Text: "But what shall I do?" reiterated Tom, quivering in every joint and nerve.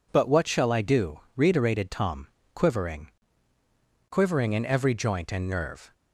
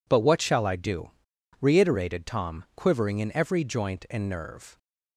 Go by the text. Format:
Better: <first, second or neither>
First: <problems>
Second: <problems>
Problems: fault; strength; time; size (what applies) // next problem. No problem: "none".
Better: second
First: says "quivering" twice; at 4.0 s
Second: none